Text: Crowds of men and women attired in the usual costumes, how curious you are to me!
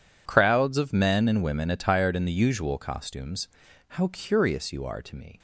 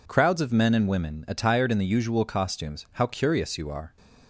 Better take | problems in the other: first | stops before "to me"; at 3.9 s

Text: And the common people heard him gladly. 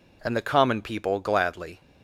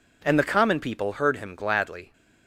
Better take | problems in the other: second | skips "heard him"; at 1.2 s

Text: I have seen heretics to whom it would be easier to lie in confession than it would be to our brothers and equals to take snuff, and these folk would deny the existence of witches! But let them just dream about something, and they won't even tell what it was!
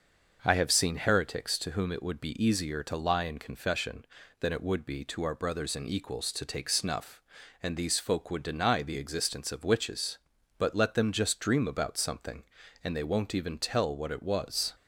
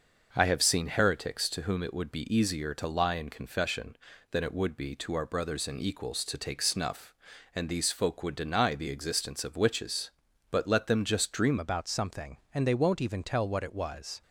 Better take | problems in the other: first | starts louder than the rest; until 1.3 s; 6 dB; also in the first // changes voice at "about"; from 11.5 s on; 2.7 s long

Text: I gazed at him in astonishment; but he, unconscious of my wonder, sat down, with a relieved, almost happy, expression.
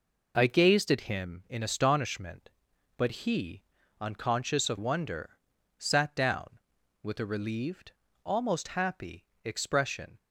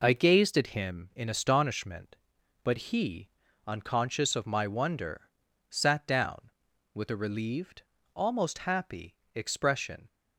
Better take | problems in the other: second | skips "my"; at 4.7 s

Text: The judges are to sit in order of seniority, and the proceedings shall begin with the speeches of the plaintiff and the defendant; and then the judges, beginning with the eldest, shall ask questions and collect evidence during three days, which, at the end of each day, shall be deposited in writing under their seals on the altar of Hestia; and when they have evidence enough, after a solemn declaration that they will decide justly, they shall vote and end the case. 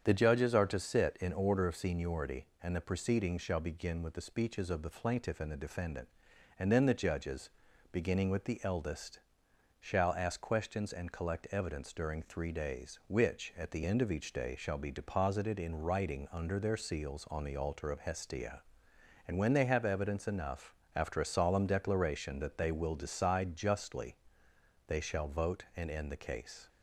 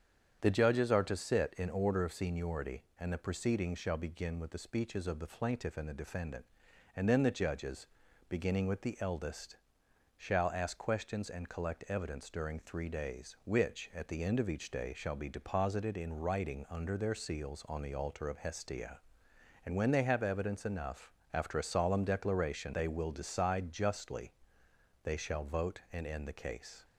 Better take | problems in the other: first | starts louder than the rest; strong; until 1.4 s; 8 dB; strong in the first // skips "that"; at 22.7 s

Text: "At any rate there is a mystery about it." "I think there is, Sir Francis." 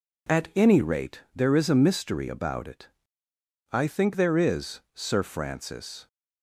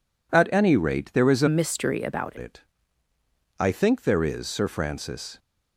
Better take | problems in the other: first | changes voice from "mystery" to "about"; from 1.4 to 2.3 s; 0.9 s long

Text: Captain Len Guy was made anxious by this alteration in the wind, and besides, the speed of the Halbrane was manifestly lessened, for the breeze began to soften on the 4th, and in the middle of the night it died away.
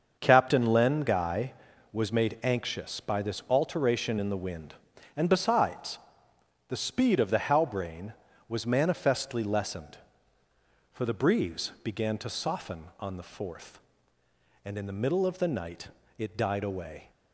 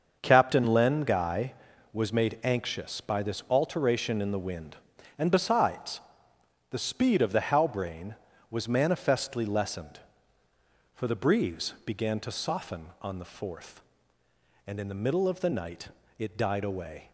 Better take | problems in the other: neither | starts louder than the rest; the same in both // pauses between "night" and "it"; slight; the same in both

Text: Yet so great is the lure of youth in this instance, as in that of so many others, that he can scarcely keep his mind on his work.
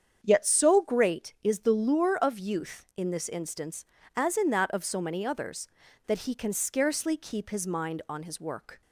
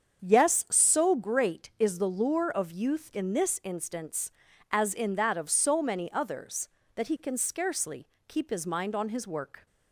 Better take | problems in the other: first | starts louder than the rest; strong; until 1.2 s; 7.5 dB; strong in the first // says "Yes" for "Yet"; at 0.2 s // pauses between "scarcely" and "keep"; slight; at 8.0 s; 0.22 s long

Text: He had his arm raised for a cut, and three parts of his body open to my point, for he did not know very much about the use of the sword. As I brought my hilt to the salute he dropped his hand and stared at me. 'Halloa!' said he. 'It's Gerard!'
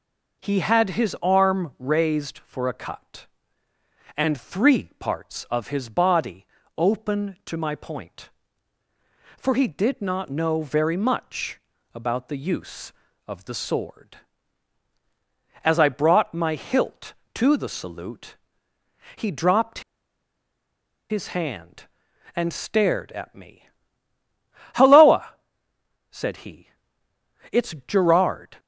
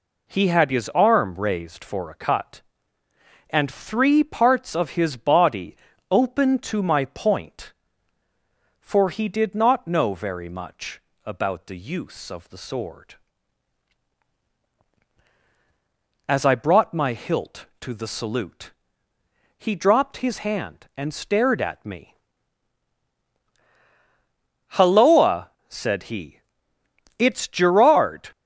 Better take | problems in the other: second | pauses between "body" and "open"; slight; at 6.4 s; 0.32 s long; slight in the second // pauses between "much" and "about"; slight; at 11.5 s; 0.34 s long; slight in the second // pauses between "salute" and "he"; noticeable; at 18.3 s; 0.80 s long; noticeable in the second // pauses between "dropped" and "his"; strong; at 19.7 s; 1.2 s long

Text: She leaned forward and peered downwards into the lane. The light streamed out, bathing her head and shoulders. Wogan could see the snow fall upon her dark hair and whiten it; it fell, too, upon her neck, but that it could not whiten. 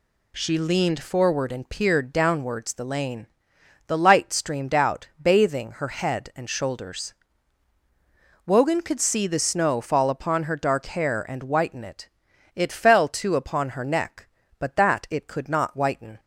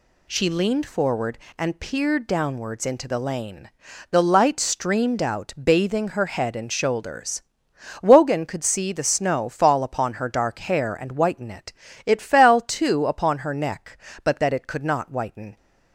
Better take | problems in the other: second | skips "into"; at 2.7 s

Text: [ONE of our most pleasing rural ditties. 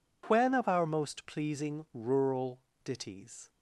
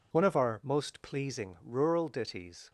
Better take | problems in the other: second | says "When" for "ONE"; at 0.2 s // pauses between "rural" and "ditties"; slight; at 2.6 s; 0.24 s long

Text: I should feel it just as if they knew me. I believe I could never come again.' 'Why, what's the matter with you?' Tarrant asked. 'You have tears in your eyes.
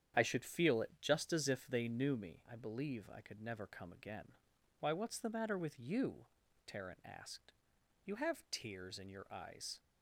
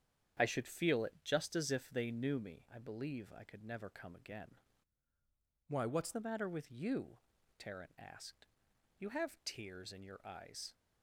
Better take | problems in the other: first | starts louder than the rest; strong; until 1.5 s; 8.5 dB; strong in the first // changes voice from "Why" to "what's"; from 5.6 to 6.1 s; 0.5 s long

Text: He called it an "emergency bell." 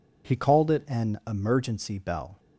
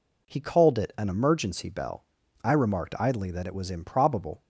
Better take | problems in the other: first | goes on to say "I remarked idly that it was improbable"; strong; from 2.4 s on; 1.9 s long

